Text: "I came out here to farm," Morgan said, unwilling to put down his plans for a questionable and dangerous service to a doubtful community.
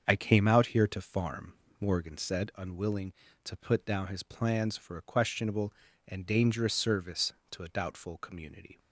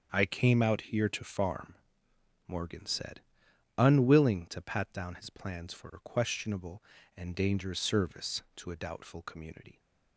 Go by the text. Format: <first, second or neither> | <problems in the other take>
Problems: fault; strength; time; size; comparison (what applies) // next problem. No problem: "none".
first | starts louder than the rest; strong; until 1.1 s; 7 dB; also in the first // says "pat" for "put"; at 4.5 s